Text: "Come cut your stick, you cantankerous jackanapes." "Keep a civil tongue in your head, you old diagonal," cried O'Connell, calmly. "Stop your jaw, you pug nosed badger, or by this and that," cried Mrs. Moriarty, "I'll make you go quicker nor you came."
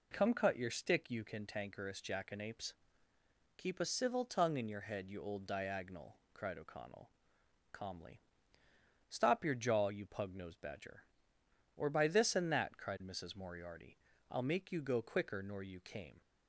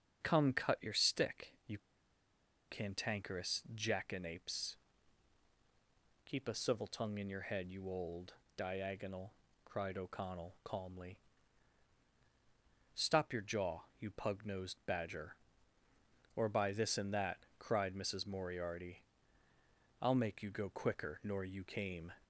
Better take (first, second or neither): first